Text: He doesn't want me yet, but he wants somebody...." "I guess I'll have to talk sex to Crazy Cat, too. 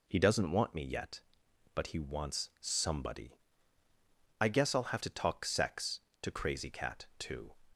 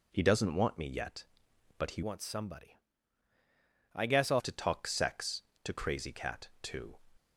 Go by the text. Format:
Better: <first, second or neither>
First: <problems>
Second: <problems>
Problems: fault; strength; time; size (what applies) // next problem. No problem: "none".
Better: first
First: none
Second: changes voice from "wants" to "I'll"; from 2.0 to 4.4 s; 2.4 s long